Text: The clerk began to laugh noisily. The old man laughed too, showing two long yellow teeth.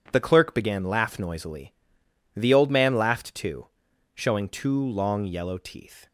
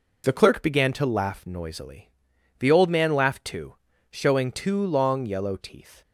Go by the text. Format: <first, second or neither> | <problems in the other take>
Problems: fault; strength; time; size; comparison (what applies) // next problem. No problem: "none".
second | skips "to"; at 0.8 s